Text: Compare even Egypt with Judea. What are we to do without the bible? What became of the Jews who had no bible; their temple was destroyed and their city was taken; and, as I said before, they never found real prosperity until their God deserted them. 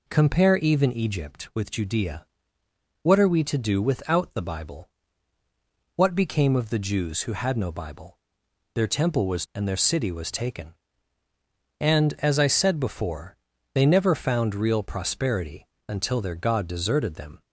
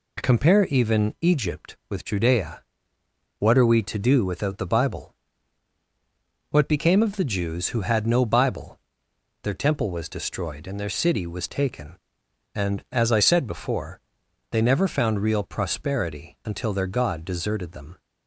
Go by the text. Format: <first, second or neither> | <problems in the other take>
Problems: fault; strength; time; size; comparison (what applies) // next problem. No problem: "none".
second | skips "destroyed"; at 9.4 s // pauses between "prosperity" and "until"; slight; at 15.6 s; 0.20 s long